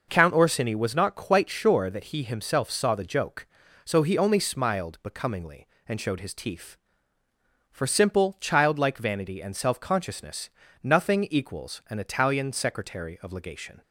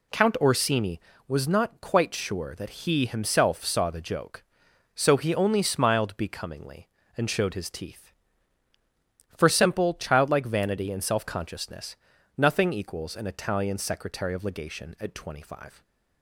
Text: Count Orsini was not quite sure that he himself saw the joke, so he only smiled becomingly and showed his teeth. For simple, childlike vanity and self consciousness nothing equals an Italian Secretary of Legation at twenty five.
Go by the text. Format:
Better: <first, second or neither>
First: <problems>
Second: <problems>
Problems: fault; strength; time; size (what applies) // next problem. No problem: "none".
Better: second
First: pauses between "consciousness" and "nothing"; slight; at 10.4 s; 0.32 s long // stops before "at twenty five"; at 13.8 s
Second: pauses between "consciousness" and "nothing"; at 11.9 s; 0.40 s long